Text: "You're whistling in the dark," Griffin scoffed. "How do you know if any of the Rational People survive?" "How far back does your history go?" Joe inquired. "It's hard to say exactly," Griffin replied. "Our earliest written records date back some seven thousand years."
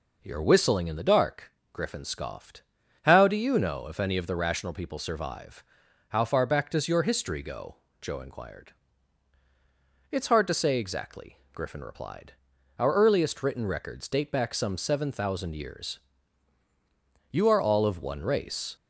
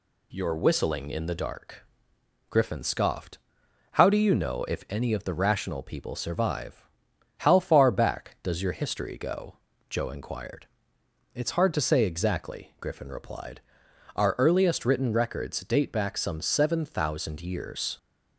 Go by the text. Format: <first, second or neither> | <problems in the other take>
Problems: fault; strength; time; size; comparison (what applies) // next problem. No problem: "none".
second | goes on to say "You are all of one race"; from 17.3 s on; 1.4 s long